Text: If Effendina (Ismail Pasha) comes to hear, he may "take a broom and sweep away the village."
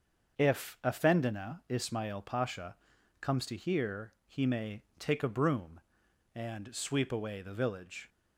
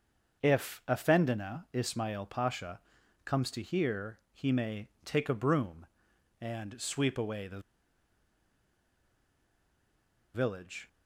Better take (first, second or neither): first